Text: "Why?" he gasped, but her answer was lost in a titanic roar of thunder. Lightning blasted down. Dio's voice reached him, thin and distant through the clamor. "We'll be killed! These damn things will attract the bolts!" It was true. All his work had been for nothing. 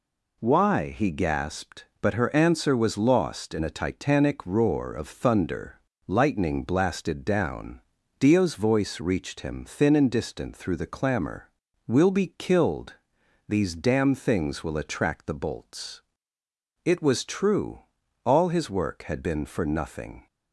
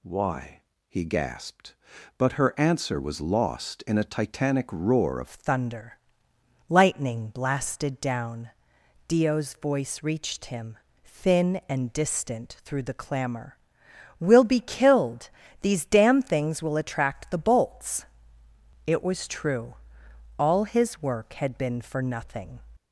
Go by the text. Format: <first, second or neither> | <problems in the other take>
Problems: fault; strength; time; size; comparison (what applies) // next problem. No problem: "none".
first | changes voice at "thunder"; from 5.2 s on; 17.4 s long